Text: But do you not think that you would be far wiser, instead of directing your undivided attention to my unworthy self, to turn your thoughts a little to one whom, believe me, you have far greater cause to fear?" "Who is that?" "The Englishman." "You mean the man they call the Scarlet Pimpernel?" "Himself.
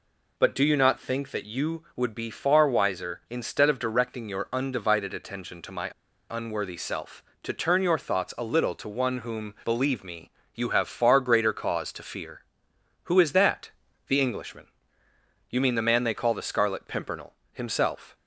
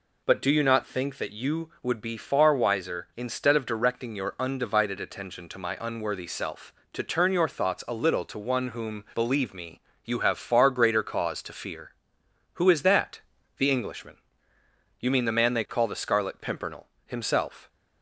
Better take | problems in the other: second | pauses between "my" and "unworthy"; at 5.9 s; 0.40 s long

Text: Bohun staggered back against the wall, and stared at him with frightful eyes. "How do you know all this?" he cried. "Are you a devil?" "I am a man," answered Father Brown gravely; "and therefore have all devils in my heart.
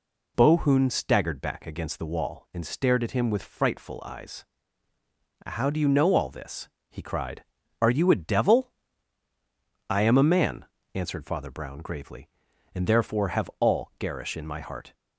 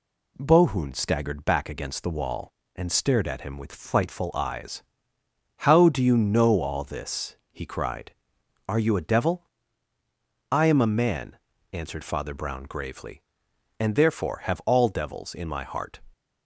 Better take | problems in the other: second | says "garish" for "devils"; at 13.9 s

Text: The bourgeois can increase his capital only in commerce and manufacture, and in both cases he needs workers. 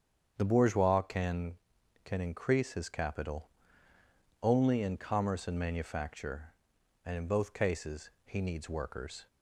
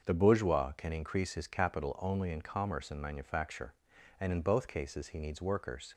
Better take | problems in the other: second | starts louder than the rest; strong; until 1.3 s; 7.5 dB; also in the second // says "can" twice; at 2.0 s // pauses between "capital" and "only"; noticeable; at 3.4 s; 0.92 s long // pauses between "cases" and "he"; slight; at 8.0 s; 0.16 s long

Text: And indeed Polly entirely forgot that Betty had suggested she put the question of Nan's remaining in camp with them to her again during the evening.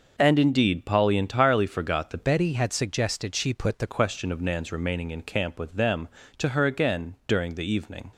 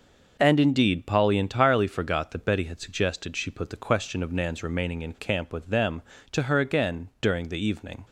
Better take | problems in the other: second | changes voice from "Betty" to "the"; from 2.2 to 3.8 s; 1.6 s long

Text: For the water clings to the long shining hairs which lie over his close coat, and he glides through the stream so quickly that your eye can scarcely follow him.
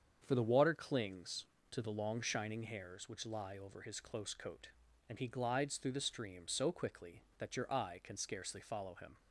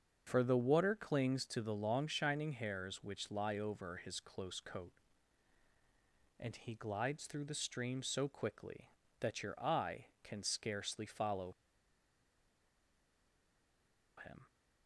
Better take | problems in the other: first | starts louder than the rest; until 1.2 s; 7 dB; strong in the first // pauses between "follow" and "him"; strong; at 11.5 s; 2.6 s long

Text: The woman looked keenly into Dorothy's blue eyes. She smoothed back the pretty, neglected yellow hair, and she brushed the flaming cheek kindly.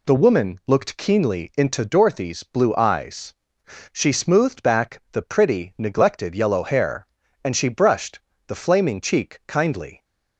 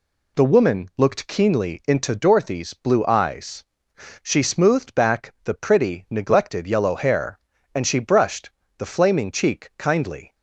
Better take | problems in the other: neither | pauses between "brushed" and "the"; slight; the same in both

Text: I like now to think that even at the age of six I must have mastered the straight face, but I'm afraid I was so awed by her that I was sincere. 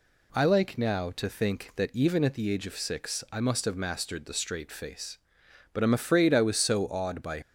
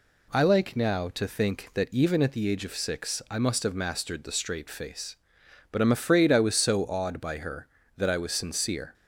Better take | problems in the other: second | stops before "her that I was sincere"; at 7.4 s

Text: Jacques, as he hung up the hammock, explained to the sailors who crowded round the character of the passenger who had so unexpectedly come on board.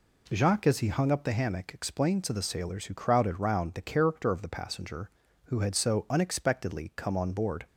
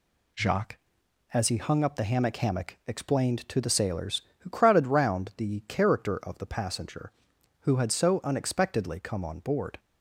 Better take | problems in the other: first | says "hammock" twice; at 2.3 s

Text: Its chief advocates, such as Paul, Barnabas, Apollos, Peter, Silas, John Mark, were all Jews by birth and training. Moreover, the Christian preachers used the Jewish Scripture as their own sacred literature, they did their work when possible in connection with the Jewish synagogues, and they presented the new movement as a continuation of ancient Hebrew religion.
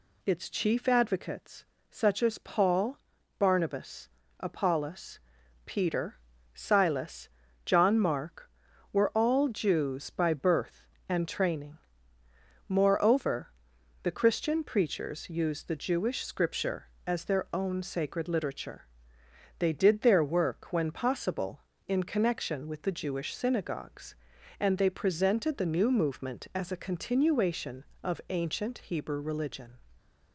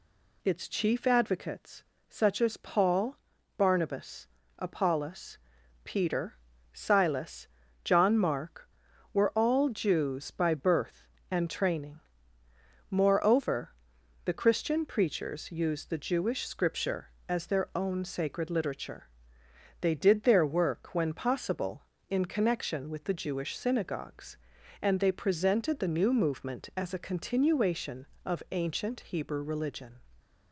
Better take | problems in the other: neither | none

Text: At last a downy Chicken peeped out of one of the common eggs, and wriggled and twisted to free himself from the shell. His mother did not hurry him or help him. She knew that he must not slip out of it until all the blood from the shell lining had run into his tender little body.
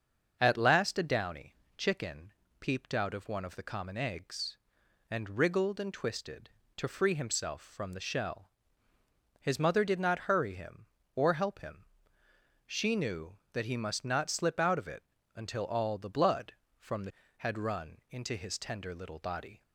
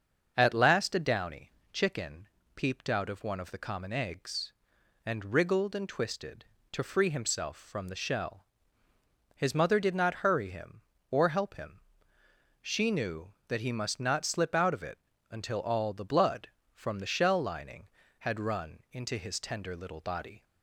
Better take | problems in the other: second | starts louder than the rest; until 1.4 s; 6.5 dB; also in the second // pauses between "downy" and "Chicken"; slight; at 1.5 s; 0.24 s long; slight in the second // pauses between "Chicken" and "peeped"; slight; at 2.3 s; 0.28 s long; slight in the second // pauses between "it" and "until"; slight; at 15.0 s; 0.32 s long; slight in the second // skips "shell lining"; at 17.2 s

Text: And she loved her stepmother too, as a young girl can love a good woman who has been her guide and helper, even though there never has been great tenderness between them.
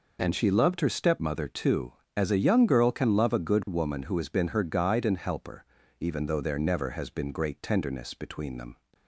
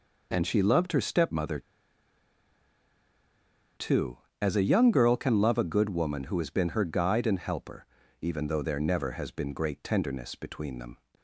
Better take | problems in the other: first | pauses between "stepmother" and "too"; strong; at 1.5 s; 2.1 s long

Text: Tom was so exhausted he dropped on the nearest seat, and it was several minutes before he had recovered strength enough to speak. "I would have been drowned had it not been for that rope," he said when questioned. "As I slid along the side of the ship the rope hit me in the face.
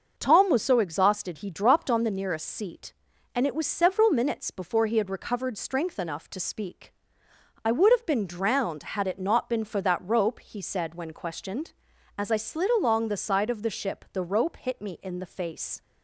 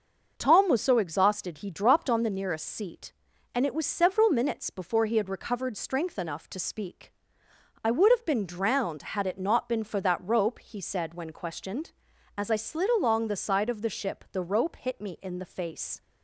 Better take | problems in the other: neither | starts louder than the rest; the same in both

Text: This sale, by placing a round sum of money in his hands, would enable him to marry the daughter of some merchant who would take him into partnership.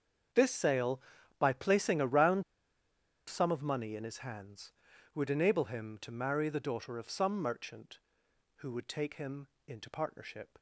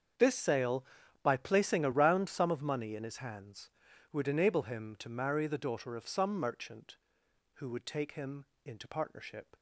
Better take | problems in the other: second | starts louder than the rest; until 1.7 s; 7 dB; also in the second // pauses between "round" and "sum"; noticeable; at 2.4 s; 0.86 s long // pauses between "him" and "into"; slight; at 9.4 s; 0.18 s long; slight in the second

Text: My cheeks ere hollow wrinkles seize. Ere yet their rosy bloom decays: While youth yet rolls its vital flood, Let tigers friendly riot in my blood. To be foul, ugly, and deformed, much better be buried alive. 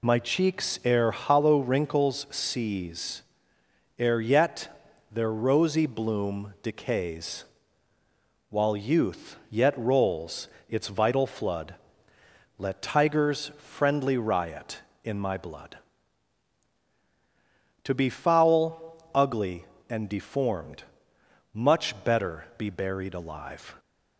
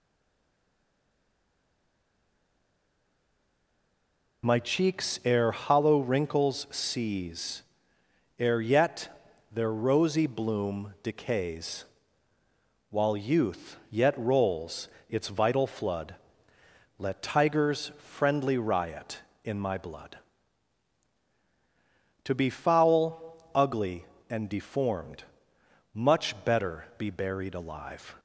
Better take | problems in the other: first | stays silent before the first word; strong; until 4.4 s; 4.4 s long // pauses between "yet" and "their"; at 9.0 s; 0.42 s long; also in the first // pauses between "rolls" and "its"; slight; at 14.8 s; 0.20 s long; slight in the first

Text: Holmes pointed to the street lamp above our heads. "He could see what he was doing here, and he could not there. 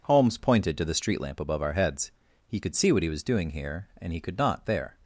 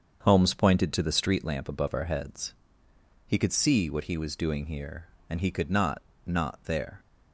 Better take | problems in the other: first | starts louder than the rest; until 1.2 s; 7 dB // says "not" twice; at 6.2 s

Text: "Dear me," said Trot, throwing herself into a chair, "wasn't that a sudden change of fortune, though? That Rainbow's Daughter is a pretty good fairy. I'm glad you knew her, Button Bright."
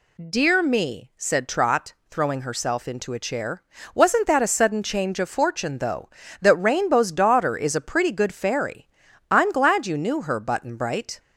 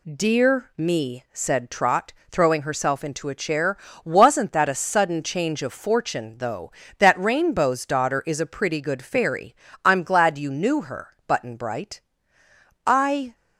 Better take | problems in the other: first | goes on to say "I"; from 12.8 s on; 0.50 s long

